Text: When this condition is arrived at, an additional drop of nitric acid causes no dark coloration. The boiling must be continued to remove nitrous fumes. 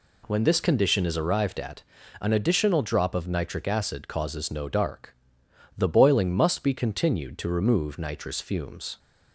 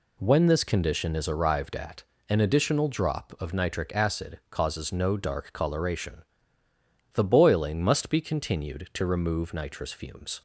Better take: second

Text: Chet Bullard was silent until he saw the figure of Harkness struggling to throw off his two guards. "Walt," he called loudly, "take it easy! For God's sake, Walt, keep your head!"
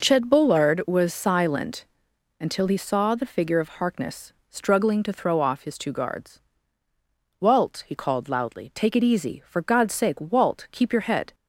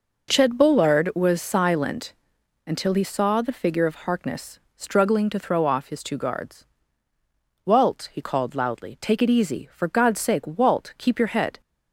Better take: neither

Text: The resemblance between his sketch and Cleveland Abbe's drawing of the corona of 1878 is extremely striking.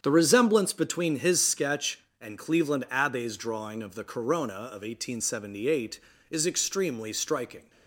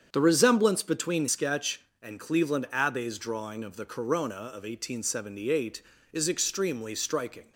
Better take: first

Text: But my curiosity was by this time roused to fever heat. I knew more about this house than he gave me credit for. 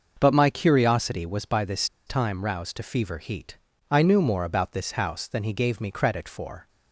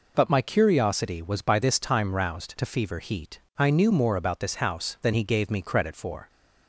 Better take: second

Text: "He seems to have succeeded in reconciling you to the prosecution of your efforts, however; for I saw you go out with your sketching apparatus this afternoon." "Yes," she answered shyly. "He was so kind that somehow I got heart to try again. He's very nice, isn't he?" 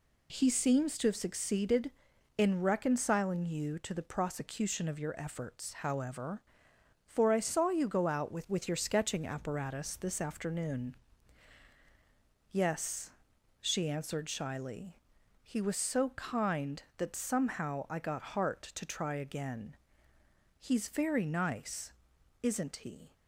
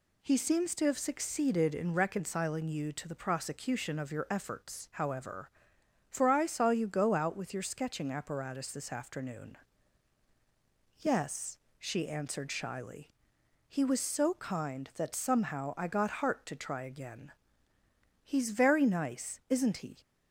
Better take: second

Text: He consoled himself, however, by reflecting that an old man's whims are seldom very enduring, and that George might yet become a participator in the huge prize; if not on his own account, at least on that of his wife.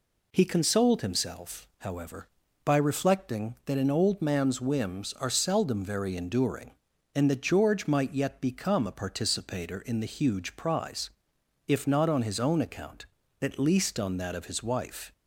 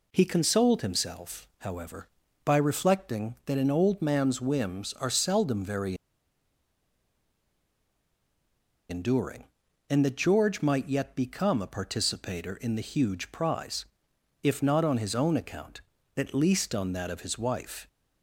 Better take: first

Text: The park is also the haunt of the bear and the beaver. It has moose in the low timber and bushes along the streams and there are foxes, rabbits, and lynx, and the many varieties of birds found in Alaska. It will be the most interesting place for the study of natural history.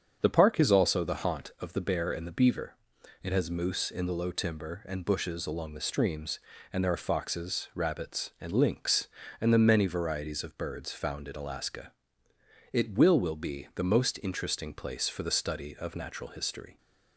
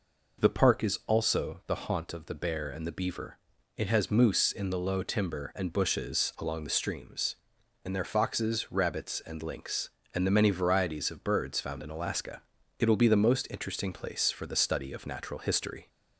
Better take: second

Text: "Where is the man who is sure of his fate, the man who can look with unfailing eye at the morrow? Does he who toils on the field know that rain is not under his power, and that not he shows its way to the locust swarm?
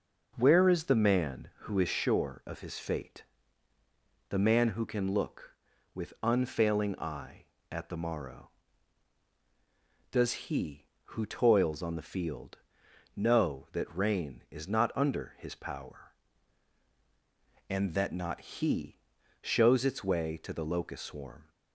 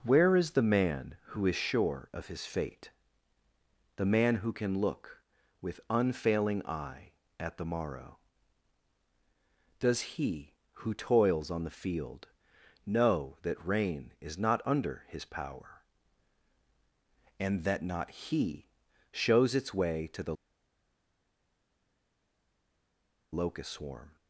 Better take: first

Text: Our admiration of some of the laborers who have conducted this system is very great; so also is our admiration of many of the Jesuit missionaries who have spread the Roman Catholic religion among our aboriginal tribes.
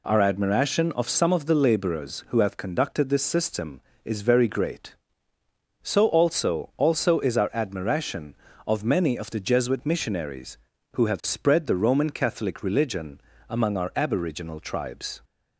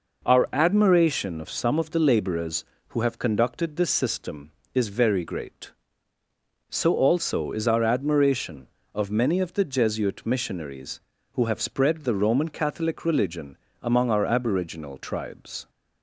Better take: second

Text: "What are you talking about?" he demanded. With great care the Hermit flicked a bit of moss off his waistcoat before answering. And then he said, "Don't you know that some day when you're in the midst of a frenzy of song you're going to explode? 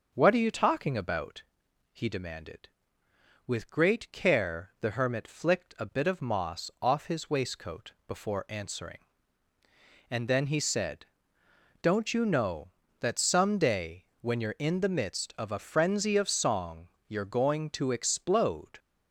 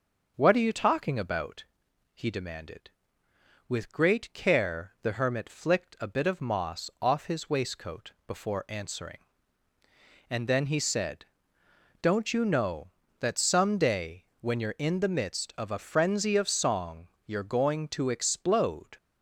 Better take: neither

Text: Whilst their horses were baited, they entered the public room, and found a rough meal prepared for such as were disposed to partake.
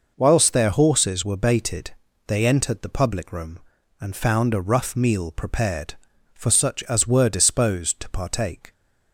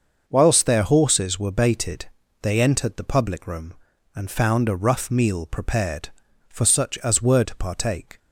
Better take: first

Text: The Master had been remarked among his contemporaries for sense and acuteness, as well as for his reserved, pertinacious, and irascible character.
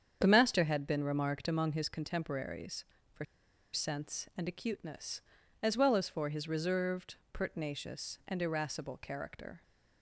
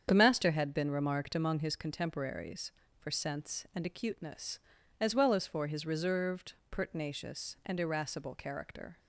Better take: second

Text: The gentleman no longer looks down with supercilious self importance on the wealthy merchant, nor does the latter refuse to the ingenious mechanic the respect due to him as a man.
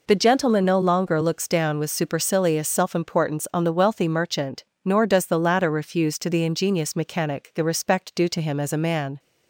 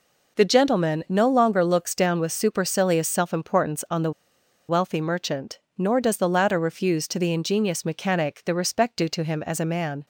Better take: first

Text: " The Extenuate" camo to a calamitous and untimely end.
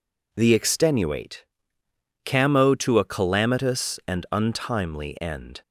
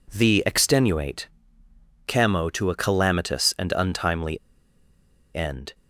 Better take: first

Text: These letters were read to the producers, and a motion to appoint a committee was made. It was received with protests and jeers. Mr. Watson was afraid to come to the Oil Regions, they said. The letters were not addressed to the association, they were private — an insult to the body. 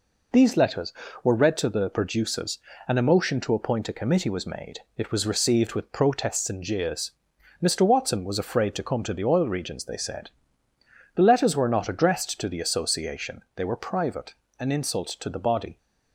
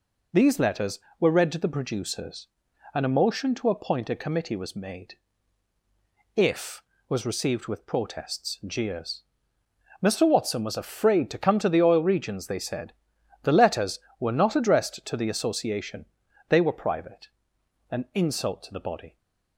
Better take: first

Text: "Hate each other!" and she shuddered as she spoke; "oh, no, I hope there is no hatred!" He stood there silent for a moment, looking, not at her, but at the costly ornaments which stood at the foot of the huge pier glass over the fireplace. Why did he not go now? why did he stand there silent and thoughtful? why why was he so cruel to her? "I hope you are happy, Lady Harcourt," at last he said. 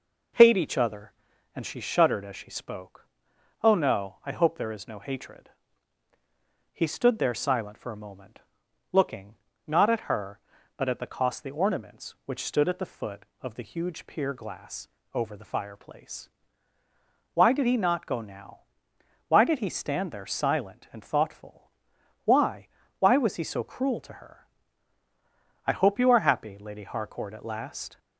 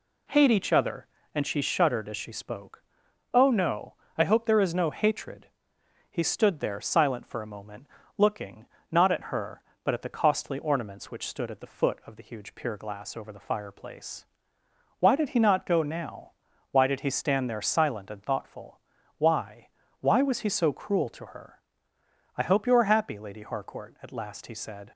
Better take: second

